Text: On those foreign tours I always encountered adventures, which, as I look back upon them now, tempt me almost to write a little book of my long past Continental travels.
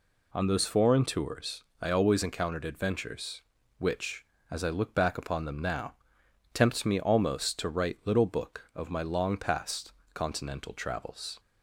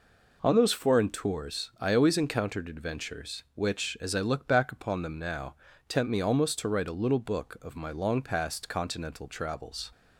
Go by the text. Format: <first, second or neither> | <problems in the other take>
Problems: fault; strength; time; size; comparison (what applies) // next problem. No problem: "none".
second | pauses between "tours" and "I"; slight; at 1.6 s; 0.18 s long // skips "a"; at 8.0 s // pauses between "past" and "Continental"; slight; at 9.9 s; 0.22 s long